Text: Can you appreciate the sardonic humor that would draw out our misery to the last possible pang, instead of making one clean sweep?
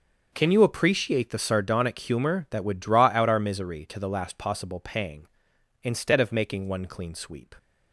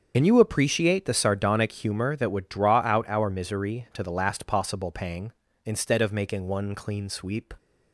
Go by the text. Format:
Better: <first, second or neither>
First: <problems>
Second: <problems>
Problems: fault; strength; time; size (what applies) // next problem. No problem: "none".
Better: first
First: starts louder than the rest; until 1.3 s; 6.5 dB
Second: loses the start of "Can"; at 0.1 s; 60 ms // starts louder than the rest; until 1.1 s; 7 dB